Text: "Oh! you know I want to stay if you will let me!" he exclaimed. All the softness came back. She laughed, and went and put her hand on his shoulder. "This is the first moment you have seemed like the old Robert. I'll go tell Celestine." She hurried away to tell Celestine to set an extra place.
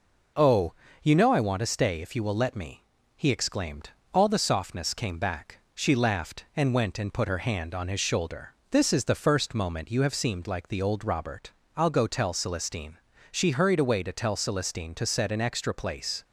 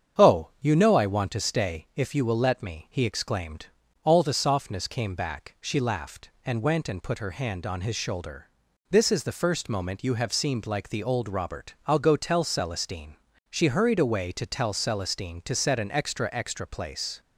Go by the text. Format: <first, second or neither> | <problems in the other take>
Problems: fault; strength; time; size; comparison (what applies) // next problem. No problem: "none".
first | starts louder than the rest; strong; until 1.3 s; 8 dB // says "extra" twice; at 16.3 s